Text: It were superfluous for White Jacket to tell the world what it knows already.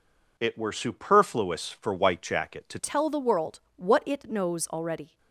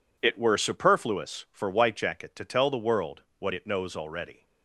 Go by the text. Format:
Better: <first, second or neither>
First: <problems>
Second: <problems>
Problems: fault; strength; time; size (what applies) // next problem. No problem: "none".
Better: second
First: changes voice at "tell"; from 2.7 s on; 2.4 s long // pauses between "world" and "what"; slight; at 3.5 s; 0.16 s long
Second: pauses between "world" and "what"; slight; at 3.2 s; 0.16 s long